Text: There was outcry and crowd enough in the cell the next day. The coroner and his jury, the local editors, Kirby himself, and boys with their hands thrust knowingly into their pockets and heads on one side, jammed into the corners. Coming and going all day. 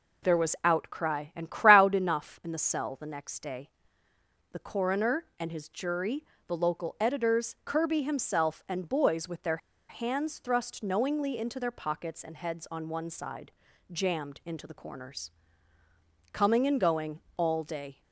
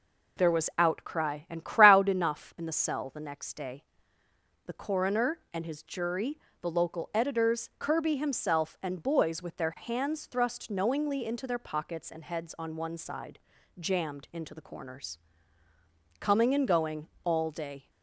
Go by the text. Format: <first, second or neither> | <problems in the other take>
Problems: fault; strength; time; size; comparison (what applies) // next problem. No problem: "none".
second | pauses between "their" and "hands"; slight; at 9.5 s; 0.31 s long // pauses between "going" and "all"; slight; at 17.2 s; 0.16 s long; slight in the second